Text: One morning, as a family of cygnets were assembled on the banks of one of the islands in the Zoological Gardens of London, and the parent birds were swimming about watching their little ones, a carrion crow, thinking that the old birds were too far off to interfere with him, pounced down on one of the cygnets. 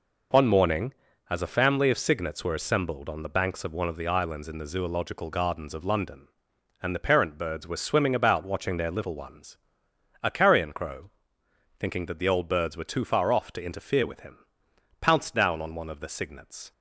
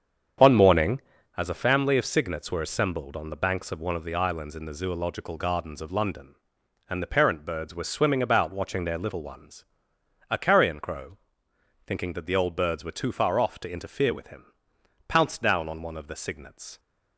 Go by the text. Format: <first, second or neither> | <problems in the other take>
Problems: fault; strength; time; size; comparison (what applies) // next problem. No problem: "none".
first | starts louder than the rest; strong; until 1.4 s; 7.5 dB